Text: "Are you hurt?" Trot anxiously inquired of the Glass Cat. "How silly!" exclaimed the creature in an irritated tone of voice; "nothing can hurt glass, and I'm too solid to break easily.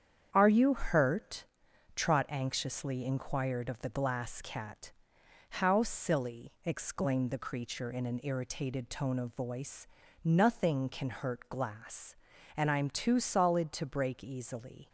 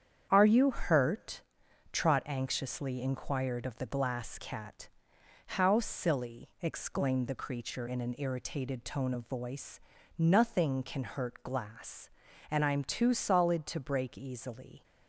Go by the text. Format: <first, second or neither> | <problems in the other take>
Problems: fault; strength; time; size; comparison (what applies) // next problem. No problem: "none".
neither | starts louder than the rest; strong; the same in both